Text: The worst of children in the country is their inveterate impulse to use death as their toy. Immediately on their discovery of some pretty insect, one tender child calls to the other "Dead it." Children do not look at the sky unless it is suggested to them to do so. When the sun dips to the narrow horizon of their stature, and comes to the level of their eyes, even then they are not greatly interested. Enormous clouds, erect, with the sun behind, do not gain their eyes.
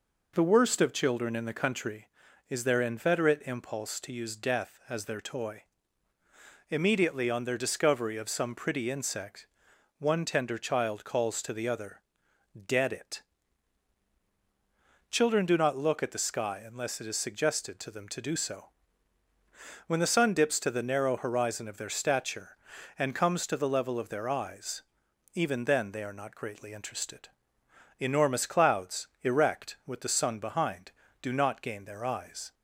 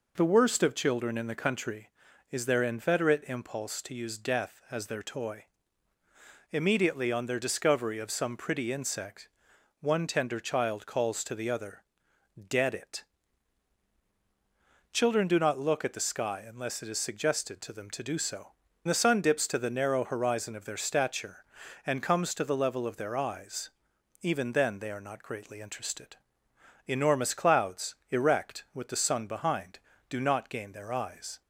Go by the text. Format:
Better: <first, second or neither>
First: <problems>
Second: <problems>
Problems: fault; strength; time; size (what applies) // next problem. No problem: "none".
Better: first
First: pauses between "other" and "Dead"; noticeable; at 12.0 s; 0.66 s long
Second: pauses between "other" and "Dead"; noticeable; at 11.8 s; 0.66 s long // skips "When"; at 18.6 s